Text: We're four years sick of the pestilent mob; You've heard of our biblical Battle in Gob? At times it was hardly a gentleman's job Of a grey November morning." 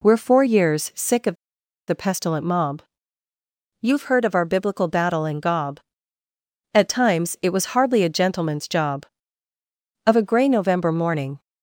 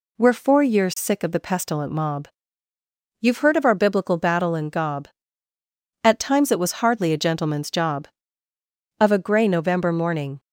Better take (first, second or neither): second